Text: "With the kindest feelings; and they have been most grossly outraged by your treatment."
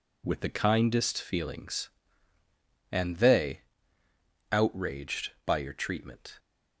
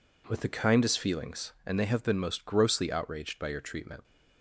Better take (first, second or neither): second